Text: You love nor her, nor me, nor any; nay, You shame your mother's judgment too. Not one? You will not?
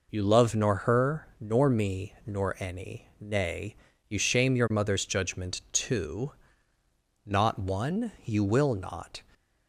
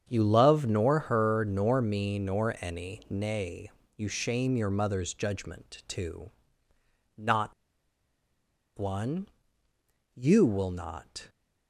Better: first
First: none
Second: starts louder than the rest; strong; until 1.0 s; 7.5 dB // pauses between "Not" and "one"; strong; at 7.5 s; 1.2 s long

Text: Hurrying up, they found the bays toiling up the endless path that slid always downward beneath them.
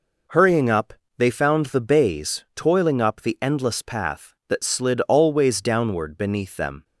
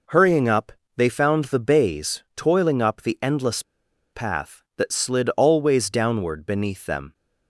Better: first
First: none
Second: pauses between "endless" and "path"; noticeable; at 3.6 s; 0.51 s long

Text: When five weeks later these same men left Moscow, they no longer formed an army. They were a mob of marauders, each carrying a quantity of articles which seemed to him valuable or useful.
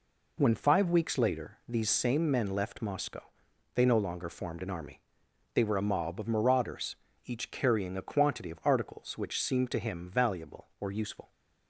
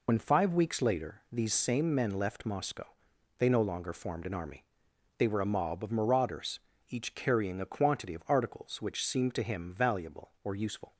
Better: first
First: none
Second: loses the start of "When"; at 0.0 s; 70 ms

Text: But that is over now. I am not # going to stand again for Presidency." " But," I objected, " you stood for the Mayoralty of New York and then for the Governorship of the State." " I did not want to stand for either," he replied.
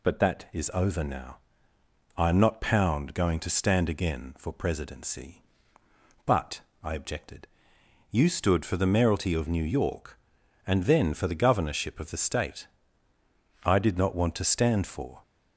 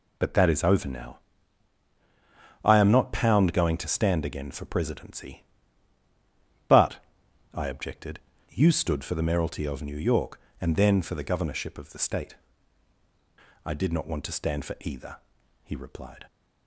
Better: second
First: stops before "either he replied"; at 15.2 s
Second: none

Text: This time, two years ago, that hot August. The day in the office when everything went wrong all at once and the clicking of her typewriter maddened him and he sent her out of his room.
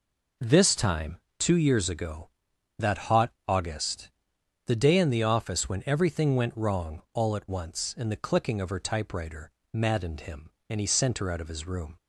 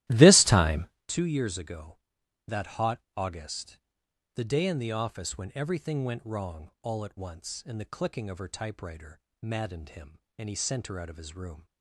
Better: first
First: pauses between "hot" and "August"; slight; at 3.3 s; 0.16 s long // pauses between "typewriter" and "maddened"; slight; at 9.5 s; 0.22 s long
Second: starts louder than the rest; strong; until 1.0 s; 15 dB // pauses between "hot" and "August"; slight; at 3.0 s; 0.16 s long // pauses between "typewriter" and "maddened"; slight; at 9.1 s; 0.22 s long

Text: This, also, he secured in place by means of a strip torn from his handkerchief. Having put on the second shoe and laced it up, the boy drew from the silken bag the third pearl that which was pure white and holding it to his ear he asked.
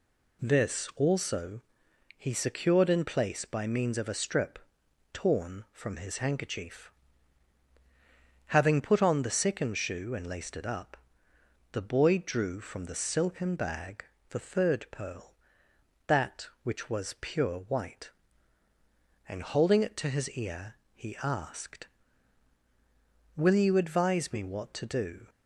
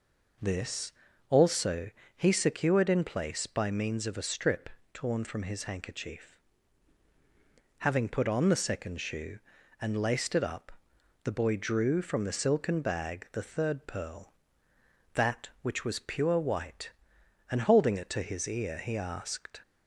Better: second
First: pauses between "strip" and "torn"; noticeable; at 4.5 s; 0.54 s long // pauses between "bag" and "the"; slight; at 14.0 s; 0.24 s long // pauses between "ear" and "he"; slight; at 20.7 s; 0.20 s long // goes on to say "Will you advise me what to do"; strong; from 23.3 s on; 1.9 s long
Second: pauses between "strip" and "torn"; slight; at 4.6 s; 0.24 s long

